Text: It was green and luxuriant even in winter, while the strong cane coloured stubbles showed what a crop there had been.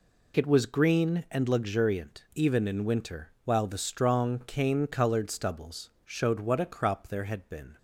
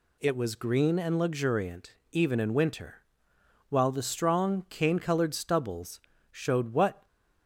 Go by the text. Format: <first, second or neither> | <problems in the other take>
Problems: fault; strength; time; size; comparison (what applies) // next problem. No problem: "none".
first | pauses between "luxuriant" and "even"; slight; at 1.9 s; 0.16 s long // pauses between "stubbles" and "showed"; slight; at 5.9 s; 0.32 s long // stops before "a crop there had been"; at 7.0 s